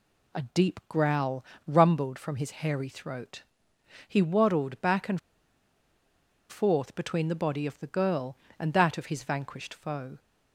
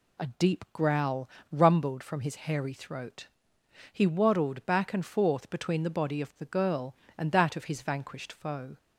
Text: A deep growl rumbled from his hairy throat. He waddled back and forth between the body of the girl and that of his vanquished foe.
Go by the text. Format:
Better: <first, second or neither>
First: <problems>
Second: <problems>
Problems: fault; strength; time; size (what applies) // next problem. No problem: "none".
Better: second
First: pauses between "growl" and "rumbled"; slight; at 1.4 s; 0.22 s long // pauses between "and" and "forth"; strong; at 5.1 s; 1.3 s long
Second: pauses between "growl" and "rumbled"; slight; at 1.2 s; 0.22 s long